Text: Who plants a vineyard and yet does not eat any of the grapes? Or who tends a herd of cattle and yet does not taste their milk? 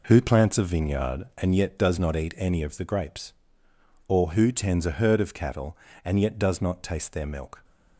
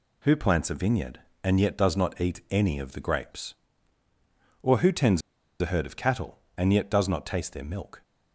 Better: first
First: none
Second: pauses between "tends" and "a"; at 5.2 s; 0.40 s long

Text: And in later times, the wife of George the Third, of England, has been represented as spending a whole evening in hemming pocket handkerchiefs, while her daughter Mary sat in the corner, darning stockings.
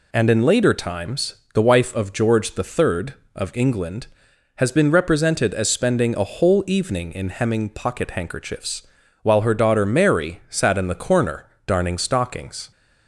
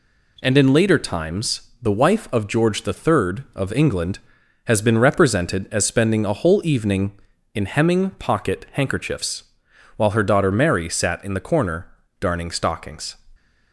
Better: neither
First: none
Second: none

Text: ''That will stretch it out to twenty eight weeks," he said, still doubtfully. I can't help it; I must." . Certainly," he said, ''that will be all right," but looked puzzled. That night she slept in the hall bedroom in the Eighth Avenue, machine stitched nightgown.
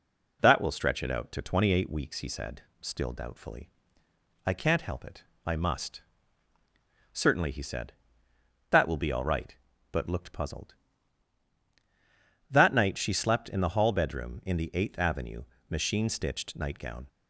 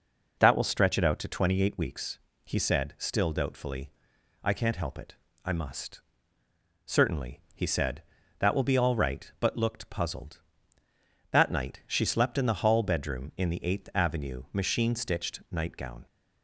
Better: neither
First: none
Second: none

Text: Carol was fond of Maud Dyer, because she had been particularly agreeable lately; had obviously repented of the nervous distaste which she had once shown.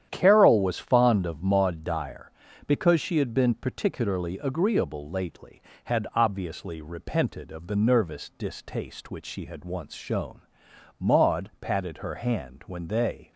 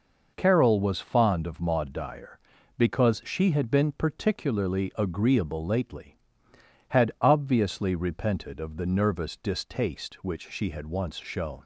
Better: second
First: starts louder than the rest; strong; until 1.1 s; 10 dB // goes on to say "Maud patted her hand when they"; strong; from 10.9 s on; 2.3 s long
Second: none

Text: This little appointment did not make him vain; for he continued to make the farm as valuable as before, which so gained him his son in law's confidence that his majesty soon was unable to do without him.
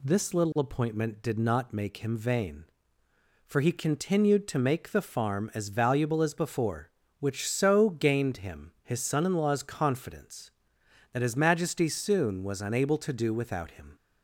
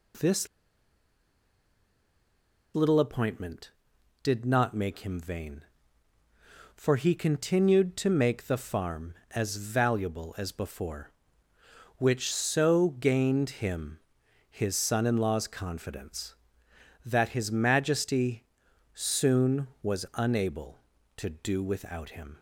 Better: first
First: none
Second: pauses between "This" and "little"; strong; at 0.4 s; 2.2 s long // pauses between "him" and "his"; noticeable; at 14.0 s; 0.50 s long // pauses between "majesty" and "soon"; noticeable; at 18.4 s; 0.50 s long

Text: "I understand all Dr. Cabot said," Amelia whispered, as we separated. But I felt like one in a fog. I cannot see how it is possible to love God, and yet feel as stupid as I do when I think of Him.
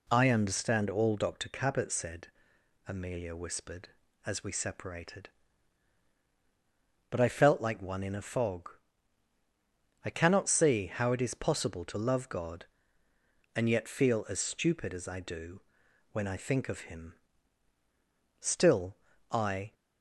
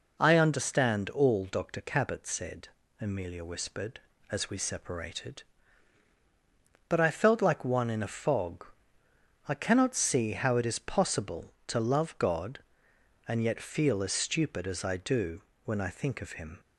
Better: second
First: pauses between "do" and "when"; noticeable; at 15.6 s; 0.50 s long // goes on to say "Still I"; from 18.3 s on; 1.3 s long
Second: pauses between "do" and "when"; slight; at 15.4 s; 0.23 s long

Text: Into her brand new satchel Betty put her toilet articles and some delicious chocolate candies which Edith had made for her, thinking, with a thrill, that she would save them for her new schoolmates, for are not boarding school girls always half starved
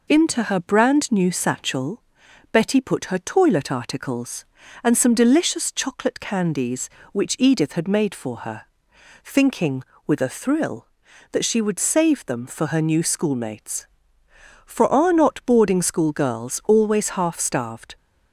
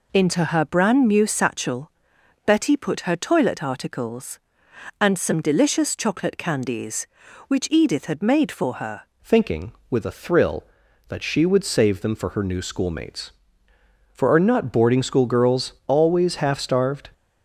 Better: first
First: pauses between "satchel" and "Betty"; noticeable; at 2.0 s; 0.52 s long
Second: pauses between "satchel" and "Betty"; noticeable; at 1.9 s; 0.52 s long // changes voice at "thinking"; from 9.2 s on; 7.8 s long

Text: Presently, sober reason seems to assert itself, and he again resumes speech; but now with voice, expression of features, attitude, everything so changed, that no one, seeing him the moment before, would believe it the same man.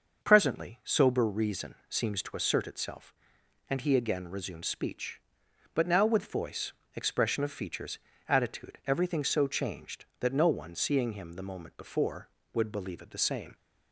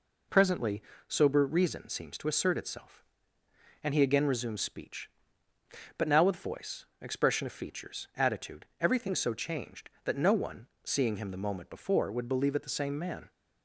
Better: second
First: starts louder than the rest; noticeable; until 1.2 s; 6 dB // pauses between "reason" and "seems"; slight; at 1.7 s; 0.16 s long // stops before "man"; at 13.5 s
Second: none

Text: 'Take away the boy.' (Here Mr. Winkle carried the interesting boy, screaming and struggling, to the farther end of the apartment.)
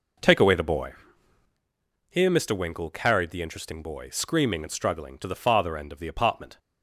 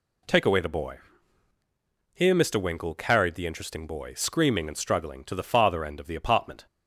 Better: second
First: starts louder than the rest; noticeable; until 1.6 s; 4.5 dB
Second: none

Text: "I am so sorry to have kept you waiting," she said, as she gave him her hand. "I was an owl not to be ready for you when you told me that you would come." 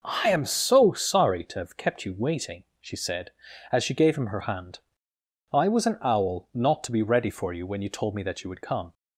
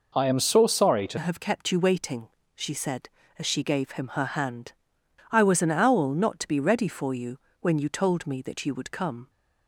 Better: first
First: none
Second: changes voice at "have"; from 1.1 s on; 8.1 s long // pauses between "you" and "when"; slight; at 7.3 s; 0.24 s long

